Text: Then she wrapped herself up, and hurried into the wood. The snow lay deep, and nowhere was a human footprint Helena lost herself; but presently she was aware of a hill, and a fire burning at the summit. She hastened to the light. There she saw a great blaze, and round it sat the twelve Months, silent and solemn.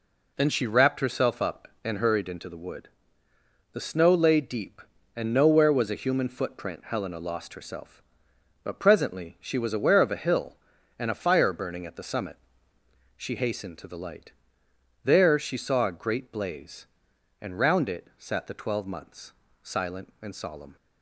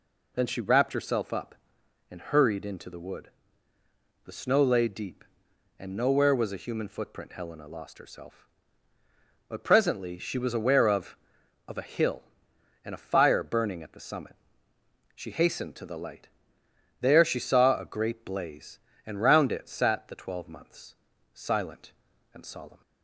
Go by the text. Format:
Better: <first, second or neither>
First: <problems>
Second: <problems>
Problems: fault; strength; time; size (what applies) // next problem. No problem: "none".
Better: first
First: none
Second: says "of" twice; at 11.6 s